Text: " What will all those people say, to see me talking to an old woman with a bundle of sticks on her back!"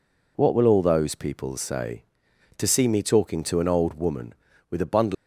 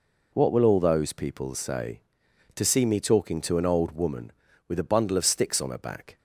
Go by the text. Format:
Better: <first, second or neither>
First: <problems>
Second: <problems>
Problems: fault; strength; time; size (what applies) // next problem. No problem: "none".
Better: second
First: stops before "of sticks on her back"; at 5.1 s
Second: none